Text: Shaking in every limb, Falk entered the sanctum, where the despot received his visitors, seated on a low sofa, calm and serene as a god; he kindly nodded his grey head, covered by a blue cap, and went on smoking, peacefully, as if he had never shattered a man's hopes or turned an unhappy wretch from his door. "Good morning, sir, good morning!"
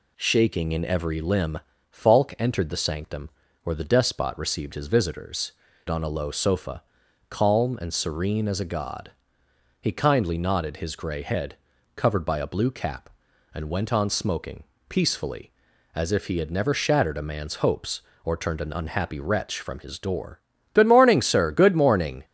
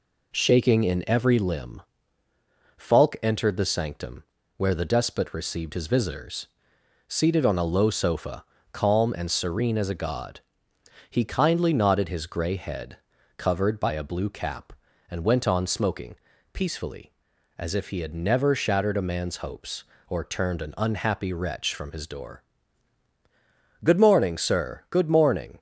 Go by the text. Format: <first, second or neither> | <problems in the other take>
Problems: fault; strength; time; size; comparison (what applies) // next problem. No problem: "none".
second | skips "seated"; at 5.7 s